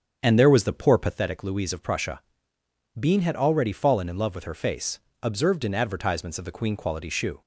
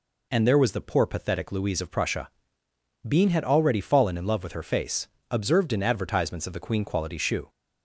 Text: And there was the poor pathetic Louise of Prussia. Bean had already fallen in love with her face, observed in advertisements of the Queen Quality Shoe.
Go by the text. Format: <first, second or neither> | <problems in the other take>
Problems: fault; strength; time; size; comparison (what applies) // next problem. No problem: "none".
second | starts louder than the rest; strong; until 1.2 s; 7.5 dB